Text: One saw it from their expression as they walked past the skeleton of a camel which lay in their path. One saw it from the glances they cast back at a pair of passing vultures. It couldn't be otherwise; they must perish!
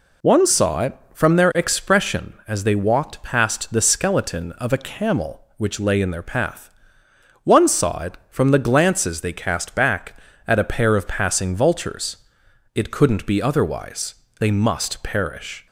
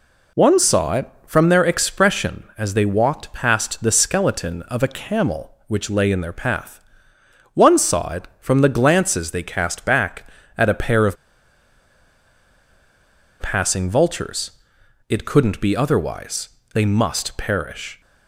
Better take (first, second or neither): first